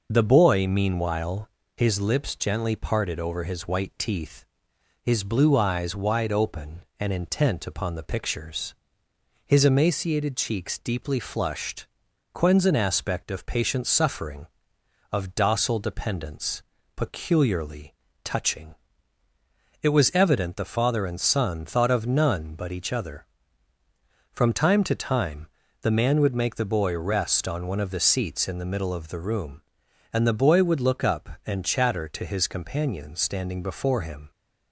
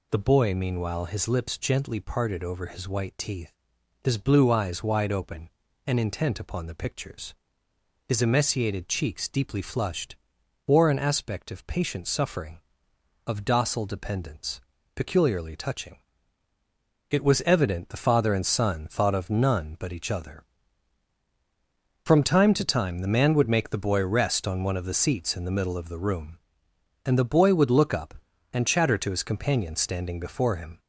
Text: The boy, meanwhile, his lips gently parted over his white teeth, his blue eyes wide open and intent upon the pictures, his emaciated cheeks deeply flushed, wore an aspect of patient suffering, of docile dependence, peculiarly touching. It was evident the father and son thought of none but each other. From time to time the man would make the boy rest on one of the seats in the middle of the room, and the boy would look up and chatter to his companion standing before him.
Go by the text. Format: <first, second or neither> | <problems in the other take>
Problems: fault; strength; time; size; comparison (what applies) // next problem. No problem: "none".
second | says "quens" for "wore"; at 12.3 s // pauses between "peculiarly" and "touching"; slight; at 17.9 s; 0.30 s long // pauses between "time" and "the"; slight; at 25.4 s; 0.32 s long